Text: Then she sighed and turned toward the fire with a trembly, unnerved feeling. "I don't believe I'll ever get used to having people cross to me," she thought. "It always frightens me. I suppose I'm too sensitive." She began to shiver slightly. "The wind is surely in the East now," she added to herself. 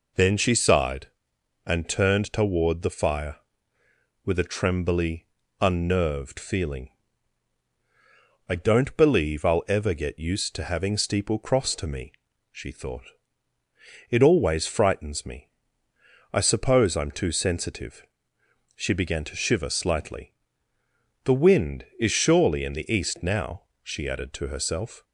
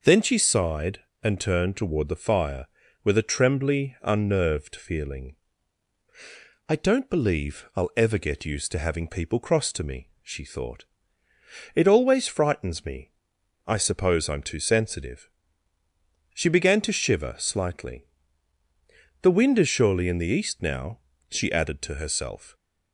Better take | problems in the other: second | says "steeple" for "people"; at 10.9 s

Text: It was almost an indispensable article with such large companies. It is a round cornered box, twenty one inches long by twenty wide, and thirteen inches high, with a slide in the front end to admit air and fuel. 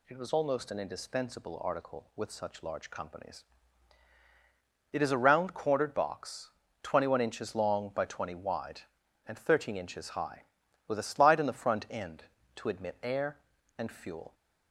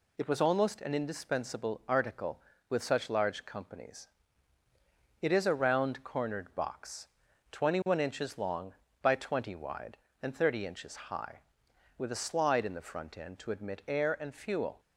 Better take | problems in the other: first | says "thirty" for "thirteen"; at 10.3 s

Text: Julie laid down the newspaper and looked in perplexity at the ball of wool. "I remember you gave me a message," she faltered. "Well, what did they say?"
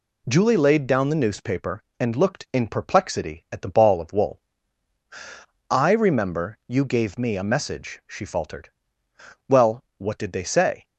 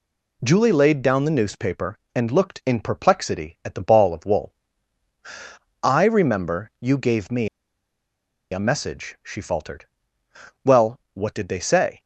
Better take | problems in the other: first | pauses between "me" and "a"; at 7.4 s; 1.0 s long

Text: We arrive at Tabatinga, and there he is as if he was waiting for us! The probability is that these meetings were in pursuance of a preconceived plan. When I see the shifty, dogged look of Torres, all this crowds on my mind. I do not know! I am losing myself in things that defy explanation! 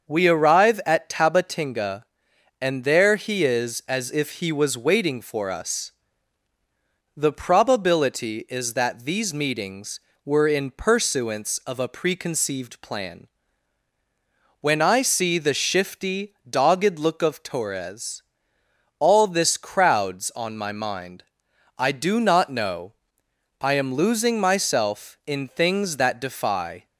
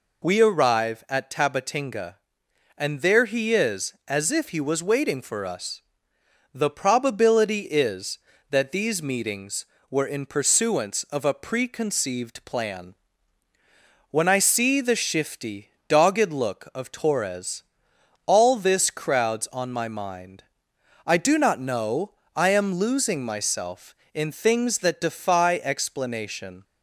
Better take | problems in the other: second | starts louder than the rest; until 1.1 s; 6.5 dB // stops before "explanation"; at 26.8 s

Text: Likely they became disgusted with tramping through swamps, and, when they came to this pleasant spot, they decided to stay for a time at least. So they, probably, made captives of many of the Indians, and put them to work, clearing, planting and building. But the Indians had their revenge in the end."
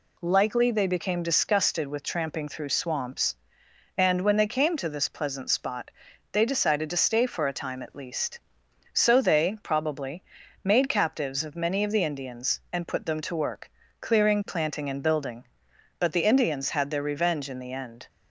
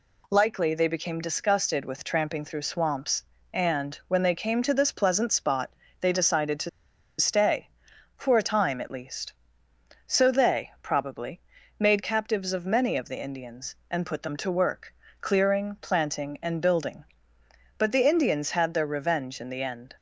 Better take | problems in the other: first | pauses between "to" and "stay"; noticeable; at 6.6 s; 0.50 s long

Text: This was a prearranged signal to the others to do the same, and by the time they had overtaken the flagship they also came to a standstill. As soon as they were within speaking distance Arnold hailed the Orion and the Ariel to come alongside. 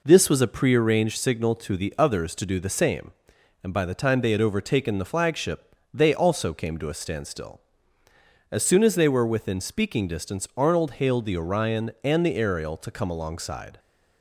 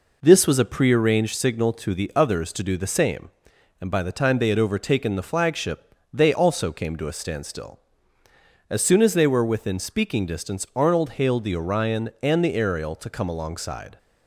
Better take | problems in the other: neither | pauses between "flagship" and "they"; slight; the same in both

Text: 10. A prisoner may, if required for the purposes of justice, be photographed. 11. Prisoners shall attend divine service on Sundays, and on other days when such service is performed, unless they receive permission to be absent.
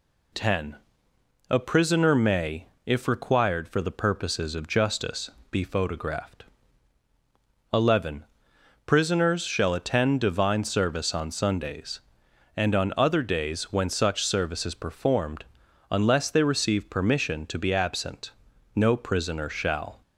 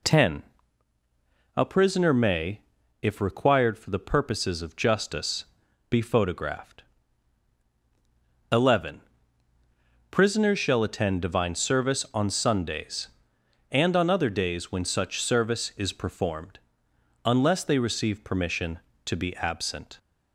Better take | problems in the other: second | goes on to say "No prisoner shall"; noticeable; from 18.7 s on; 1.2 s long

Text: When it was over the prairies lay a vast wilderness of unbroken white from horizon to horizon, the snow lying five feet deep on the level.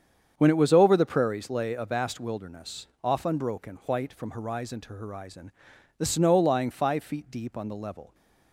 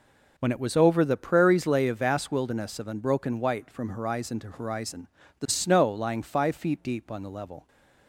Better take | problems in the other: second | starts louder than the rest; strong; until 1.3 s; 7.5 dB // says "off" for "of"; at 3.0 s

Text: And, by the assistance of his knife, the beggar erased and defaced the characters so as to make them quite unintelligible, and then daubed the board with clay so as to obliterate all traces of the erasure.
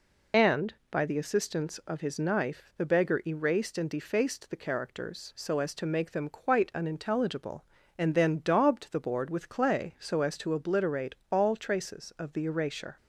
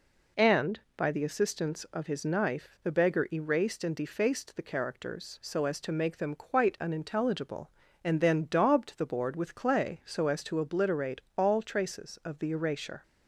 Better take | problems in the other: second | loses the start of "And"; at 0.3 s; 40 ms // pauses between "obliterate" and "all"; slight; at 11.1 s; 0.16 s long; slight in the second

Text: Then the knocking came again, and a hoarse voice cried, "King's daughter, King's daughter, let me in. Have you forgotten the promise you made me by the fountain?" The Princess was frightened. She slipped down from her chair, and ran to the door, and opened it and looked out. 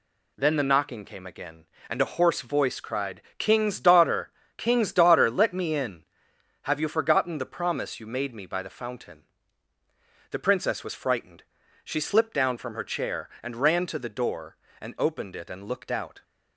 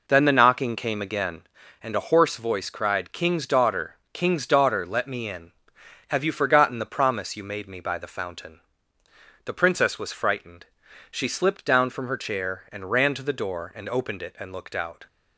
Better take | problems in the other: first | starts louder than the rest; noticeable; until 1.8 s; 4.5 dB

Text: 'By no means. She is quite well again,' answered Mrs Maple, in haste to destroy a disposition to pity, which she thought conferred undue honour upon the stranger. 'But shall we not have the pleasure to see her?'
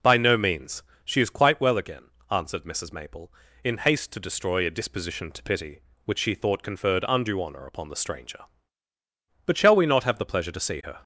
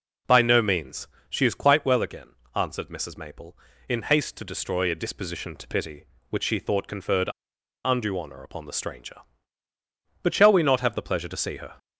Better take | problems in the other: first | pauses between "conferred" and "undue"; noticeable; at 7.2 s; 0.56 s long

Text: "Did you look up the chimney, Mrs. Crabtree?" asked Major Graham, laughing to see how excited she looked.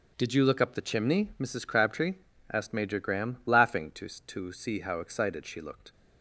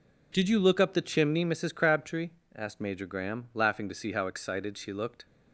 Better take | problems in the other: second | starts louder than the rest; until 1.1 s; 7 dB // says "to" twice; at 4.0 s

